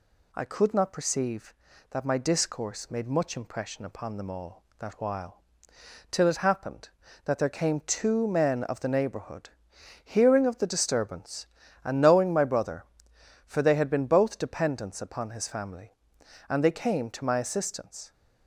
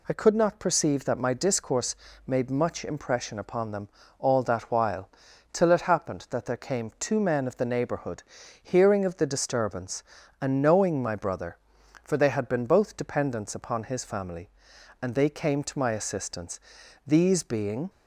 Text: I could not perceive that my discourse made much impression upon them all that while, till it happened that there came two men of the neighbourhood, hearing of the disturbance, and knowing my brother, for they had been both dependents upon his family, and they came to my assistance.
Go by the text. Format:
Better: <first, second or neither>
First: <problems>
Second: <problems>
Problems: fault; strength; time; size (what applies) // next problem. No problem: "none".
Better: first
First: none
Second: pauses between "discourse" and "made"; slight; at 1.9 s; 0.32 s long // pauses between "them" and "all"; slight; at 3.8 s; 0.32 s long // goes on to say "These being"; noticeable; from 17.0 s on; 0.84 s long